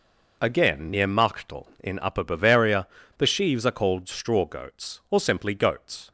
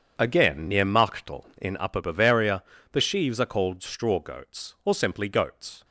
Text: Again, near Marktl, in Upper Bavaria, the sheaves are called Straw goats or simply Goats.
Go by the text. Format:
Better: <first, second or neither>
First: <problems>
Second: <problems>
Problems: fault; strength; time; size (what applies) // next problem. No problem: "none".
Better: first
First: none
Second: starts louder than the rest; strong; until 1.8 s; 7.5 dB